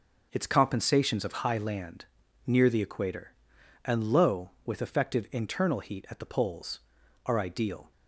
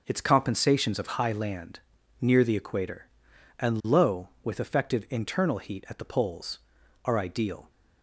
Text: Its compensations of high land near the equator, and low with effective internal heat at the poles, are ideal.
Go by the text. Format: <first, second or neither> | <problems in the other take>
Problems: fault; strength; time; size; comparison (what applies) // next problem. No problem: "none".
neither | pauses between "land" and "near"; the same in both